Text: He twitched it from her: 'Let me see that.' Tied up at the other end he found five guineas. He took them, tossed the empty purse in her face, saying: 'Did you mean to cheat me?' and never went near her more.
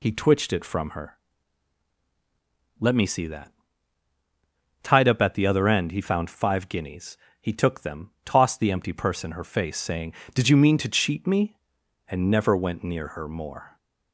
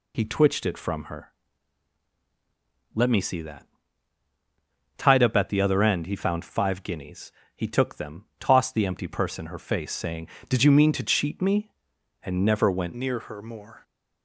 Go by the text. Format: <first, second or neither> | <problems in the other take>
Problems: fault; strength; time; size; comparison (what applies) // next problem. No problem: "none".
first | changes voice at "near"; from 12.9 s on; 0.9 s long